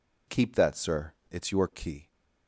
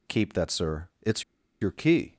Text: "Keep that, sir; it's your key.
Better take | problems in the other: first | pauses between "it's" and "your"; at 1.2 s; 0.39 s long

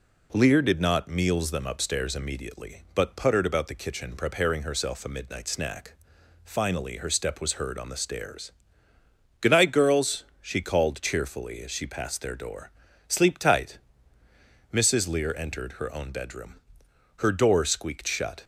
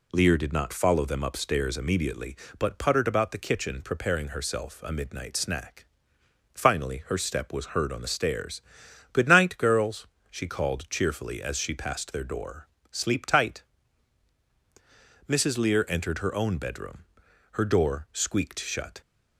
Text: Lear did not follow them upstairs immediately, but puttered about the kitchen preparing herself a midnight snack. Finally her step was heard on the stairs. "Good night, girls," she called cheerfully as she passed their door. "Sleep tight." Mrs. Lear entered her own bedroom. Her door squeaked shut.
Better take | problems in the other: second | says "meals" for "follow"; at 1.0 s

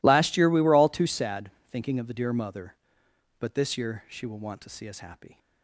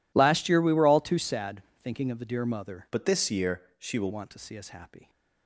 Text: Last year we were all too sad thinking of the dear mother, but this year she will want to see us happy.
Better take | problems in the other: first | pauses between "sad" and "thinking"; slight; at 1.6 s; 0.20 s long; slight in the first // changes voice from "but" to "will"; from 2.9 to 4.1 s; 1.2 s long // pauses between "year" and "she"; slight; at 3.6 s; 0.16 s long

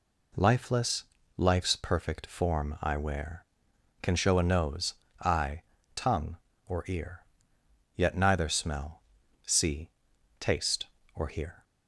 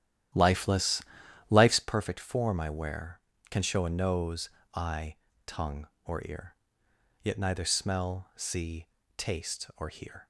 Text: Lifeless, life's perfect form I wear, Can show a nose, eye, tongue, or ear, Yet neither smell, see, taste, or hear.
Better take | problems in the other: first | starts louder than the rest; strong; until 1.9 s; 12 dB

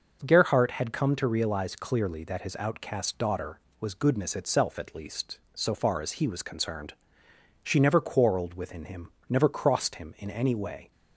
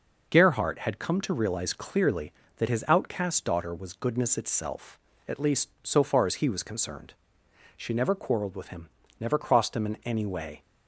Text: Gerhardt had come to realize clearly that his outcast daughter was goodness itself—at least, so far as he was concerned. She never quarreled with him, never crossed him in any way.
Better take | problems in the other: second | says "within" for "with"; at 8.5 s

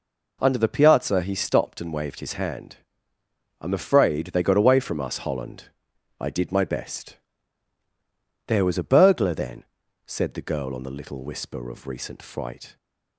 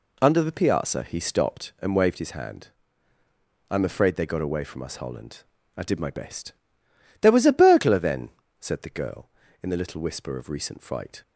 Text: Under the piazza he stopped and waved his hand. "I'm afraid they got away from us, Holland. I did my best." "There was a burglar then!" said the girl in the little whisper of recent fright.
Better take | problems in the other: second | says "on" for "in"; at 10.7 s

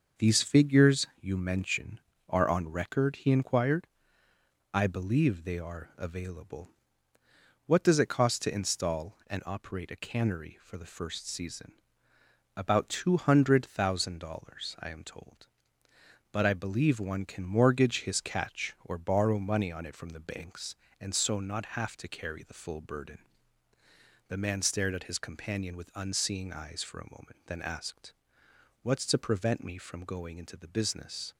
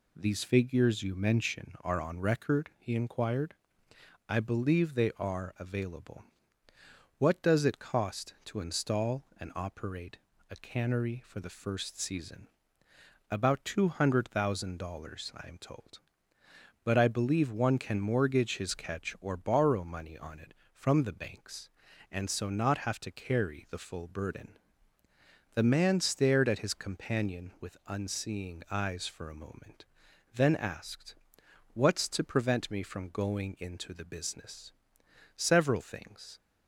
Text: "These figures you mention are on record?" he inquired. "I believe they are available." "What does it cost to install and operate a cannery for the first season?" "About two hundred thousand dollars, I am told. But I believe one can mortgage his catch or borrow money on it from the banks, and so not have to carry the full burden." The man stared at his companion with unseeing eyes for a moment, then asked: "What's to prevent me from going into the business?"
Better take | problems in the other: first | pauses between "operate" and "a"; slight; at 10.1 s; 0.32 s long // goes on to say "Several things"; noticeable; from 35.3 s on; 1.0 s long

